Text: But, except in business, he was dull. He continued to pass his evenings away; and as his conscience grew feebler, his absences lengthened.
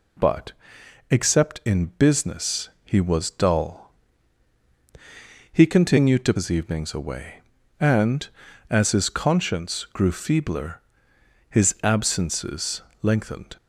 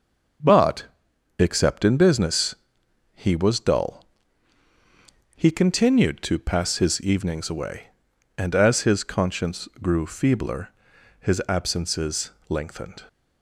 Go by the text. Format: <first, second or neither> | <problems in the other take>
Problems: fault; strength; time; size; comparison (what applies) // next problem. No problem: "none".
second | skips "pass"; at 6.3 s // pauses between "absences" and "lengthened"; slight; at 12.8 s; 0.18 s long; slight in the second